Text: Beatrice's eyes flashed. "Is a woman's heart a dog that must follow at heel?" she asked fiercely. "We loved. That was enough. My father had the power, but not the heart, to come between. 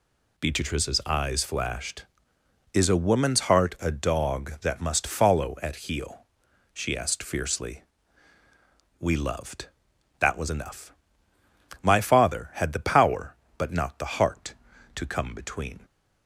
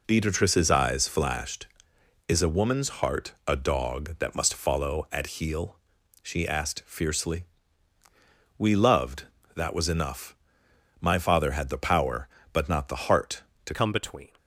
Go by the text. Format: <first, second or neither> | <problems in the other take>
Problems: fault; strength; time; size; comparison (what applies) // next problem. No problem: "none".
first | changes voice at "come"; from 13.7 s on; 0.6 s long